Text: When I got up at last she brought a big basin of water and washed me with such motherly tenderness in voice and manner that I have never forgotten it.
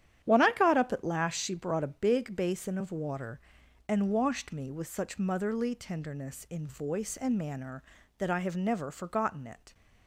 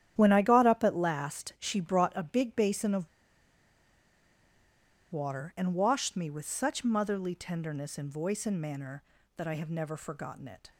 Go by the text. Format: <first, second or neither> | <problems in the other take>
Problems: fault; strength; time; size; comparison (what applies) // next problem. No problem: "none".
first | starts louder than the rest; strong; until 1.1 s; 10.5 dB; strong in the first // pauses between "of" and "water"; strong; at 3.0 s; 2.0 s long